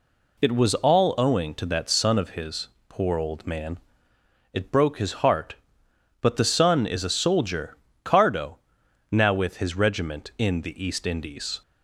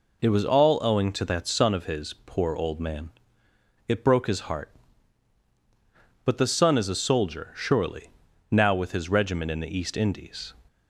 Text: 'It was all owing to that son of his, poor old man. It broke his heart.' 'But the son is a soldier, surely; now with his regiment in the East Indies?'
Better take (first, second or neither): second